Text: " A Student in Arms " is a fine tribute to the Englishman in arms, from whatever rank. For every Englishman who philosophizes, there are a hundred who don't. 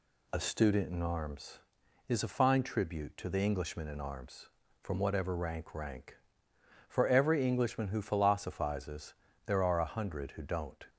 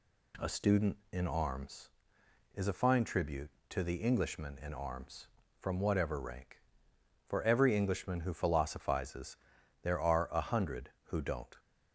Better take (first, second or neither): second